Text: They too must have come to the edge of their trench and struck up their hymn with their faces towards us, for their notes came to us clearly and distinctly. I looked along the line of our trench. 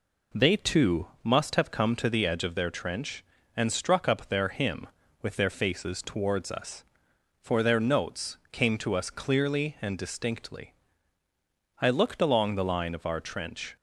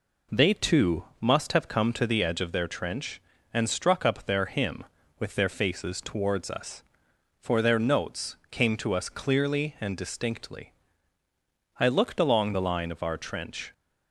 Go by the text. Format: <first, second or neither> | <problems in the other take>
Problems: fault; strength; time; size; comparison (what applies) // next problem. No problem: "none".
neither | pauses between "too" and "must"; slight; the same in both